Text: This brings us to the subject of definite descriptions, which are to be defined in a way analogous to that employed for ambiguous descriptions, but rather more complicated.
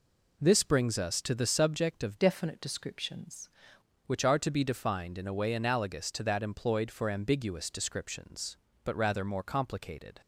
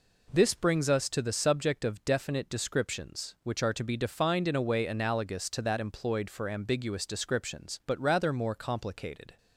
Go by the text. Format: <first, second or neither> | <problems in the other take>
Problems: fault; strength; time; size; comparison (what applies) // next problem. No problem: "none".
second | changes voice from "definite" to "descriptions"; from 2.1 to 3.4 s; 1.3 s long